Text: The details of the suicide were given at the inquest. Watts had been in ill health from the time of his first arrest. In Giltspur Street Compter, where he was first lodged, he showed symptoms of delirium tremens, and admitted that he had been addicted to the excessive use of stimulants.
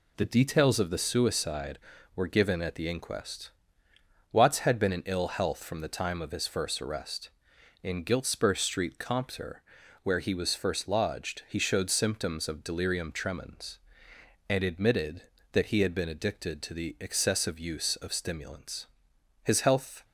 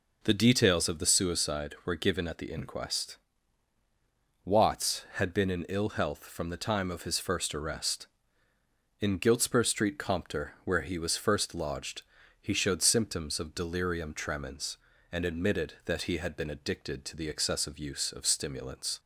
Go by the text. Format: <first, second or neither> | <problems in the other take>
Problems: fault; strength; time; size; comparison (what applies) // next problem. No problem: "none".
second | goes on to say "His health"; noticeable; from 19.4 s on; 0.62 s long